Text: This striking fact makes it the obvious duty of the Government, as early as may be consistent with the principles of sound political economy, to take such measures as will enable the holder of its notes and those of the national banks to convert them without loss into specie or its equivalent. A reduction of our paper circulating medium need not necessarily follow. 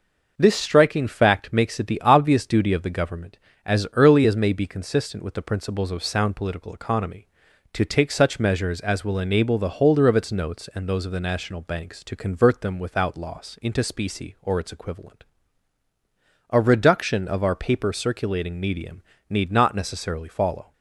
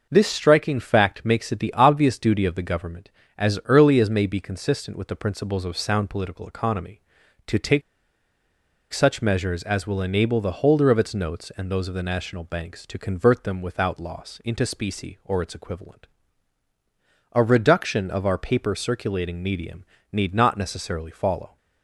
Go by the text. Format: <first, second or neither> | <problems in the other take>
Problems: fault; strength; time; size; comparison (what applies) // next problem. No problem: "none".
first | pauses between "take" and "such"; at 7.8 s; 1.1 s long // pauses between "medium" and "need"; slight; at 19.8 s; 0.28 s long; slight in the first